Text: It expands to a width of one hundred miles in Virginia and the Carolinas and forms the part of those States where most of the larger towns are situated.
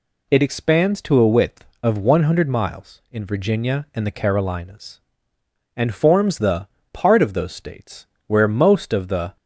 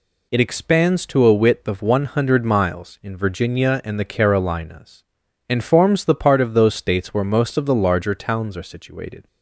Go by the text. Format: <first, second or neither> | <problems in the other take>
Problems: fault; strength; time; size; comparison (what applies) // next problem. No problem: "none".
second | pauses between "the" and "part"; slight; at 6.6 s; 0.26 s long // pauses between "States" and "where"; slight; at 8.0 s; 0.22 s long // stops before "larger towns are situated"; at 9.3 s